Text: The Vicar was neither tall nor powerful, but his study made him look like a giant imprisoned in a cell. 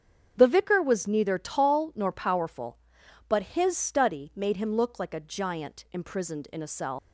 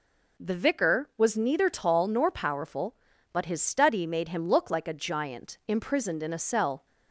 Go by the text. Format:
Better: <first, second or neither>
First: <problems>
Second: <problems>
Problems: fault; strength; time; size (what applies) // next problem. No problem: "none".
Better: second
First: starts louder than the rest; strong; until 1.3 s; 7.5 dB // leaves "cell" unfinished; at 6.9 s; 95 ms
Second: none